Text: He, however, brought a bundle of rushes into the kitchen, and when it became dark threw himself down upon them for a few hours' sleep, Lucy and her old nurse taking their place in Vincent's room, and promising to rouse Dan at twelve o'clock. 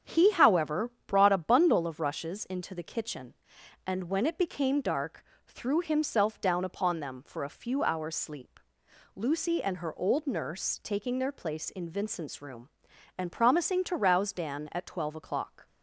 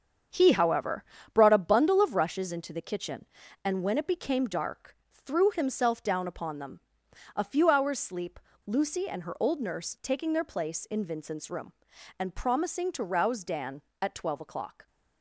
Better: first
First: starts louder than the rest; strong; until 1.2 s; 8 dB // pauses between "dark" and "threw"; slight; at 5.2 s; 0.24 s long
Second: starts louder than the rest; strong; until 1.6 s; 7.5 dB // pauses between "dark" and "threw"; slight; at 4.9 s; 0.28 s long // skips "for"; at 7.0 s

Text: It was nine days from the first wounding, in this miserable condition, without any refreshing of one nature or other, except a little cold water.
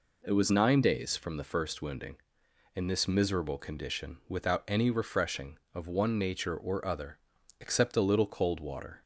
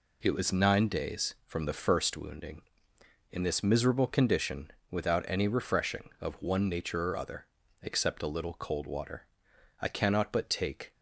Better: first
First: none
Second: goes on to say "I cannot but take"; noticeable; from 9.7 s on; 1.1 s long

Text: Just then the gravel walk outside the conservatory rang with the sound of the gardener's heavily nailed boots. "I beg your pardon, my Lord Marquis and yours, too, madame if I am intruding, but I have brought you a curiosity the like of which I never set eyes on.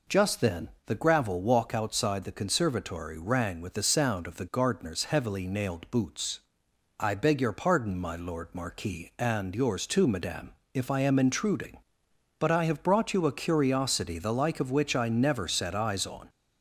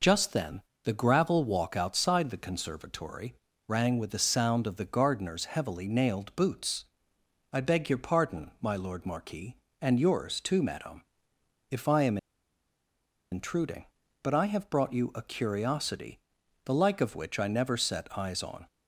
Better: first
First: pauses between "then" and "the"; slight; at 0.6 s; 0.16 s long // pauses between "madame" and "if"; slight; at 10.5 s; 0.22 s long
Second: pauses between "then" and "the"; slight; at 0.6 s; 0.22 s long // pauses between "conservatory" and "rang"; slight; at 3.3 s; 0.34 s long // pauses between "madame" and "if"; noticeable; at 11.0 s; 0.66 s long // pauses between "am" and "intruding"; at 12.1 s; 1.1 s long // pauses between "curiosity" and "the"; noticeable; at 16.1 s; 0.46 s long

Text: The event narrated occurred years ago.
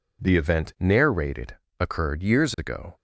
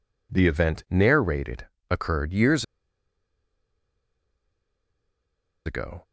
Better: first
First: pauses between "narrated" and "occurred"; slight; at 1.5 s; 0.24 s long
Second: pauses between "narrated" and "occurred"; slight; at 1.6 s; 0.24 s long // pauses between "years" and "ago"; strong; at 2.6 s; 3.0 s long

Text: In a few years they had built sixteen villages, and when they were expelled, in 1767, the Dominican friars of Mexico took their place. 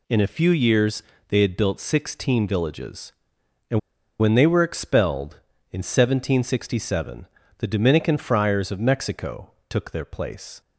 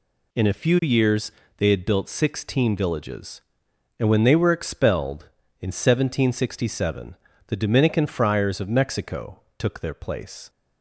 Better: second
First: pauses between "years" and "they"; slight; at 1.0 s; 0.26 s long // pauses between "and" and "when"; at 3.7 s; 0.40 s long // pauses between "Mexico" and "took"; slight; at 9.5 s; 0.18 s long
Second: pauses between "years" and "they"; slight; at 1.3 s; 0.26 s long // pauses between "Mexico" and "took"; slight; at 9.4 s; 0.18 s long

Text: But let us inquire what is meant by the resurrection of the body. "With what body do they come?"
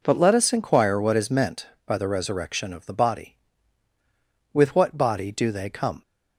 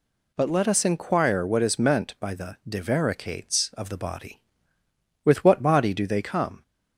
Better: first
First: none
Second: says "divaricates" for "resurrection"; at 2.6 s

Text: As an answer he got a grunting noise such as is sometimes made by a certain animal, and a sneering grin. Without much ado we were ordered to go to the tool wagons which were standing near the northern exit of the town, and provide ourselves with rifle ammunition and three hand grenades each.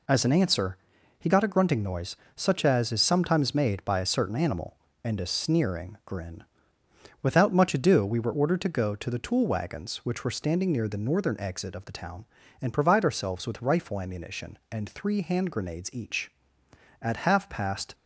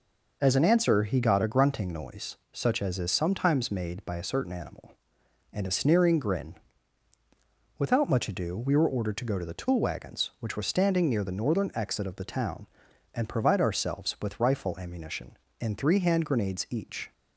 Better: second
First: pauses between "answer" and "he"; at 0.7 s; 0.40 s long // pauses between "noise" and "such"; slight; at 2.1 s; 0.20 s long // goes on to say "At half past"; noticeable; from 16.9 s on; 0.94 s long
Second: none

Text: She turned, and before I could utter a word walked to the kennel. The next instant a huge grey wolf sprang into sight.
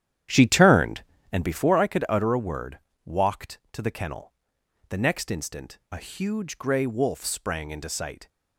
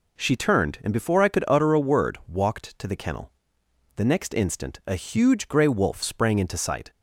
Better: second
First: starts louder than the rest; strong; until 1.8 s; 10.5 dB // pauses between "word" and "walked"; slight; at 2.7 s; 0.26 s long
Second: none

